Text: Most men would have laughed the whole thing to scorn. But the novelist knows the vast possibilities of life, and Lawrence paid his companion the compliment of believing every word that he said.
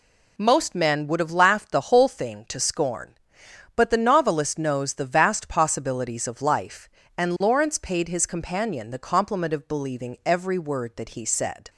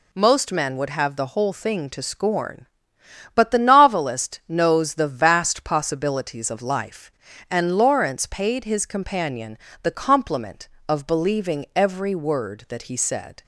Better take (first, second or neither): first